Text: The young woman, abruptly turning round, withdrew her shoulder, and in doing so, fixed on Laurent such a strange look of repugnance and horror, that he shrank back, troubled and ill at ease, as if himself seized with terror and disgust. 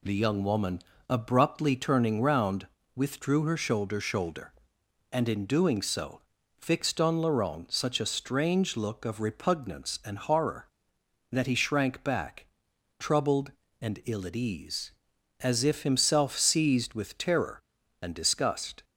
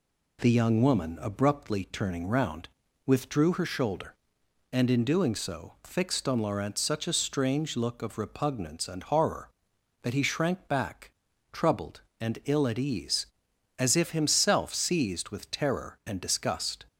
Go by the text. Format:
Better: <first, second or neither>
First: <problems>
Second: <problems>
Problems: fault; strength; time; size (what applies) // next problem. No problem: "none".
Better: second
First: says "shoulder" twice; at 4.0 s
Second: none